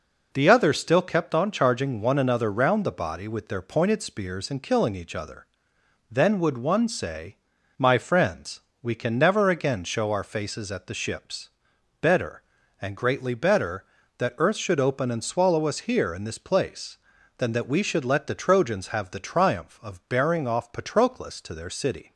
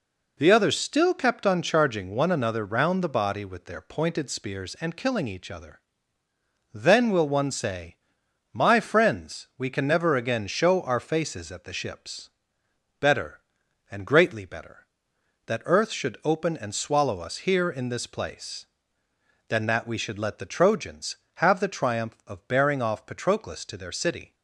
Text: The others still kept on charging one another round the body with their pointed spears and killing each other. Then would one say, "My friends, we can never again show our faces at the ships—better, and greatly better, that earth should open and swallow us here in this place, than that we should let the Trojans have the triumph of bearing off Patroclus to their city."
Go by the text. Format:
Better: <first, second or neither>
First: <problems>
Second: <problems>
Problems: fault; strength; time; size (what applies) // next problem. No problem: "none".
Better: first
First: none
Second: says "will" for "would"; at 7.1 s